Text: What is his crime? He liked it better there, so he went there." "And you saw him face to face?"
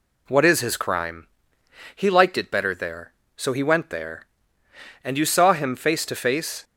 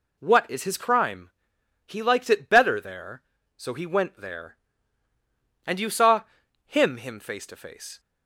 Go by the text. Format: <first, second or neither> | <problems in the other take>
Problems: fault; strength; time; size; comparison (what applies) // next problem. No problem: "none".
first | pauses between "saw" and "him"; at 6.2 s; 0.42 s long // says "him" twice; at 6.9 s